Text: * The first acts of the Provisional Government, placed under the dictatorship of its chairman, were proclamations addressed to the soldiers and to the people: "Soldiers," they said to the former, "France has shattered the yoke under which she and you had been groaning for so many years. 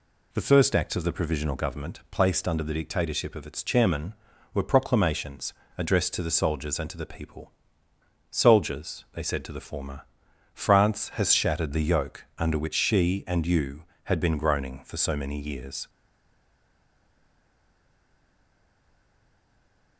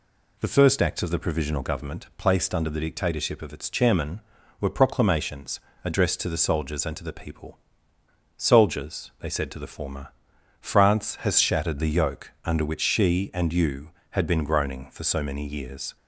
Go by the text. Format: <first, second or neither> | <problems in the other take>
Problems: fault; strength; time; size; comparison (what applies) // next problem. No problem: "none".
second | pauses between "proclamations" and "addressed"; slight; at 5.5 s; 0.24 s long; slight in the second // stays silent after the last word; strong; from 15.8 s on; 4.1 s long